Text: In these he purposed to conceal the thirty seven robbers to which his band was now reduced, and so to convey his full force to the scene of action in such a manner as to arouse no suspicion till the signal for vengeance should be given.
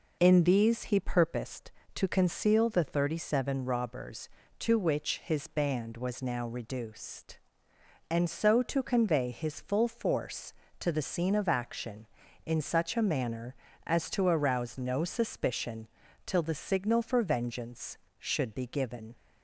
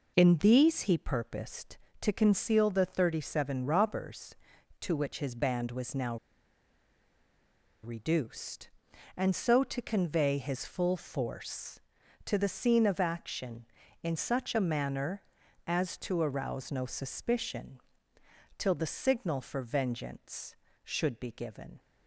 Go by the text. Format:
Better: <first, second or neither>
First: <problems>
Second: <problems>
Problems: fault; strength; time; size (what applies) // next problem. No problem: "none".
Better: first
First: pauses between "suspicion" and "till"; at 15.8 s; 0.40 s long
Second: pauses between "now" and "reduced"; strong; at 6.1 s; 1.6 s long // pauses between "suspicion" and "till"; noticeable; at 17.7 s; 0.78 s long